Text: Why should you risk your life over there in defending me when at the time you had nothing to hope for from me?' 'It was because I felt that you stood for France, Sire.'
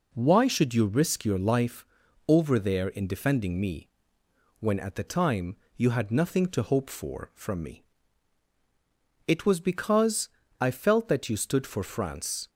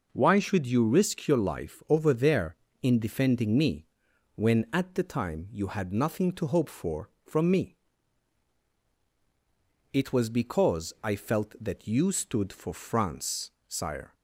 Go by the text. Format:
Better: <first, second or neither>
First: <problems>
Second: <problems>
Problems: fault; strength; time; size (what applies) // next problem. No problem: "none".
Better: second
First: pauses between "life" and "over"; at 1.8 s; 0.42 s long // pauses between "me" and "when"; noticeable; at 3.8 s; 0.72 s long // pauses between "time" and "you"; slight; at 5.5 s; 0.22 s long // pauses between "because" and "I"; slight; at 10.2 s; 0.32 s long // stops before "Sire"; at 12.4 s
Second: pauses between "me" and "when"; noticeable; at 3.8 s; 0.48 s long